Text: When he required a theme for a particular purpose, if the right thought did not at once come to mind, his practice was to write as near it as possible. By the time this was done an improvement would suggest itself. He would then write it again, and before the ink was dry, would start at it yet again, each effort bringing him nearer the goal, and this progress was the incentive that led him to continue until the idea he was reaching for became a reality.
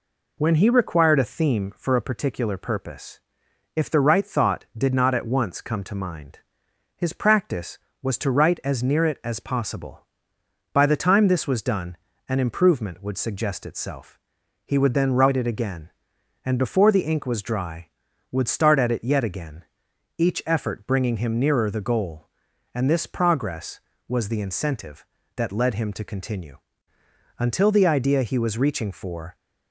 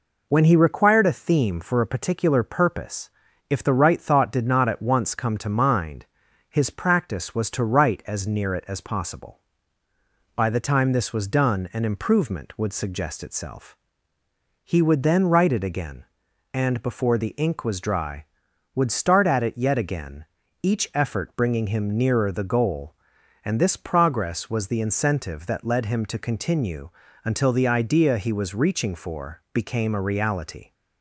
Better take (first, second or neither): second